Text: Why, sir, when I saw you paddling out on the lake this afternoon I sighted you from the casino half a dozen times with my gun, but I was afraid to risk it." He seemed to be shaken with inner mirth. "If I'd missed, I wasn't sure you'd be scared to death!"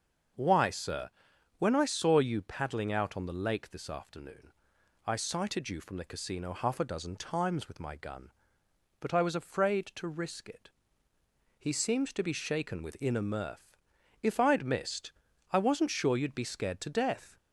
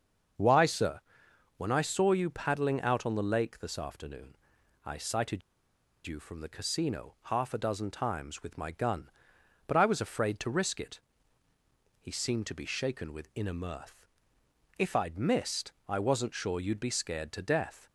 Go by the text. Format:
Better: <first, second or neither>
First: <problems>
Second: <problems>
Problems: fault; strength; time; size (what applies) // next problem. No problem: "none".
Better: first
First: starts louder than the rest; until 1.8 s; 6.5 dB // pauses between "afternoon" and "I"; noticeable; at 4.5 s; 0.54 s long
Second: starts louder than the rest; until 1.9 s; 6.5 dB // pauses between "afternoon" and "I"; noticeable; at 4.3 s; 0.48 s long // pauses between "sighted" and "you"; noticeable; at 5.4 s; 0.66 s long